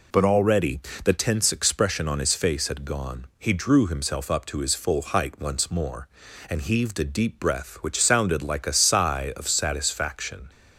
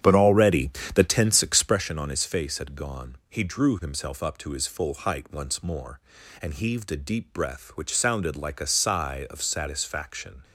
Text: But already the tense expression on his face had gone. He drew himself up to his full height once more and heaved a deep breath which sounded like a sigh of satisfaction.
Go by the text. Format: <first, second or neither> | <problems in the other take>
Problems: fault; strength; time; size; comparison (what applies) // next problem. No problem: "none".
first | starts louder than the rest; strong; until 1.9 s; 9 dB // pauses between "already" and "the"; slight; at 0.6 s; 0.26 s long; slight in the first